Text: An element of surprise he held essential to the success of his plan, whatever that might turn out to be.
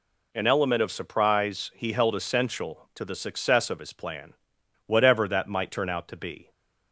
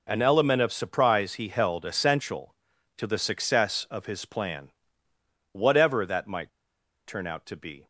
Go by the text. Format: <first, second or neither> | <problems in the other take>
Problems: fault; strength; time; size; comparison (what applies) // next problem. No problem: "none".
first | pauses between "might" and "turn"; noticeable; at 6.4 s; 0.56 s long